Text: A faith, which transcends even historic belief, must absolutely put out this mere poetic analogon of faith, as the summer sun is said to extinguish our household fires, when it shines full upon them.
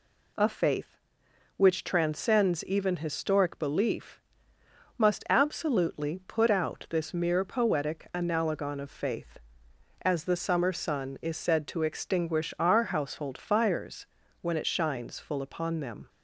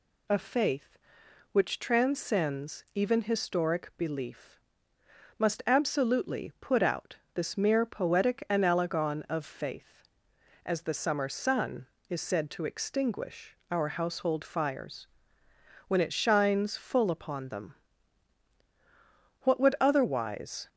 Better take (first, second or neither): first